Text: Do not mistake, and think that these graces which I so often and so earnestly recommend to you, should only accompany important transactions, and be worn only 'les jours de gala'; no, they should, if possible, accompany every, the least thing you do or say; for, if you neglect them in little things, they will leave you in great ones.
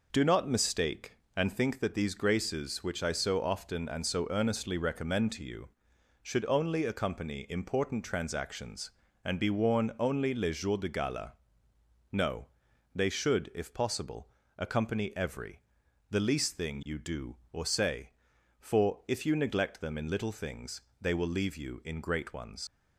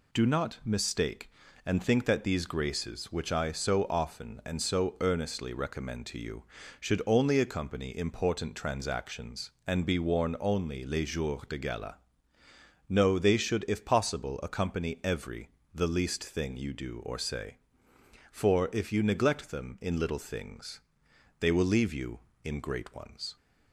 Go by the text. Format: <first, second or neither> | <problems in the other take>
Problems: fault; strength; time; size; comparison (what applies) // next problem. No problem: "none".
second | leaves "ones" unfinished; at 22.6 s; 80 ms